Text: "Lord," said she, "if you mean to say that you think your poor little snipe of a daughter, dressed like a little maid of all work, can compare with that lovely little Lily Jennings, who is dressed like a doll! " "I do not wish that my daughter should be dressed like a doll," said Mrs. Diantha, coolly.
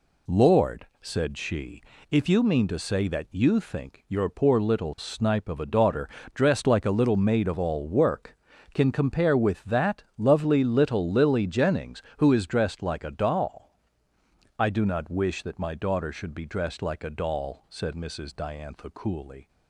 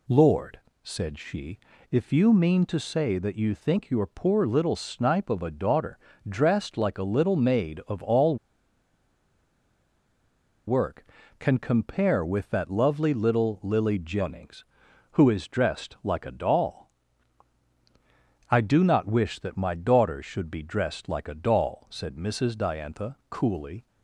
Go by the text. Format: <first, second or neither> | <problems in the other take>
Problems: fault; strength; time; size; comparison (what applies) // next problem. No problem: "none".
first | pauses between "all" and "work"; strong; at 8.3 s; 2.3 s long